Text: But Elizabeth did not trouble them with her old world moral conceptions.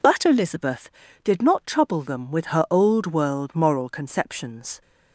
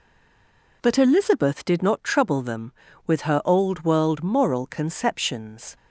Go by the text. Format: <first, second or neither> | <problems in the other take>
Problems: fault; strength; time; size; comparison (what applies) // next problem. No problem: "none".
first | stays silent before the first word; slight; until 0.8 s; 0.8 s long